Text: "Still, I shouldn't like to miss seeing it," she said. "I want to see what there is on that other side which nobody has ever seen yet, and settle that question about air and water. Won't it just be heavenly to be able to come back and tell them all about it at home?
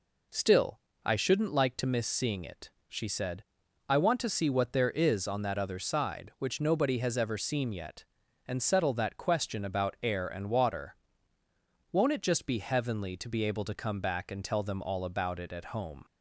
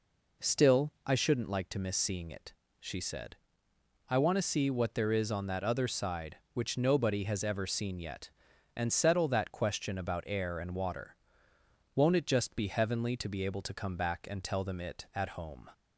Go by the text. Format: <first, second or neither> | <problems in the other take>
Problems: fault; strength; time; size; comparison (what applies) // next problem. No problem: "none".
first | skips "all about"; at 14.7 s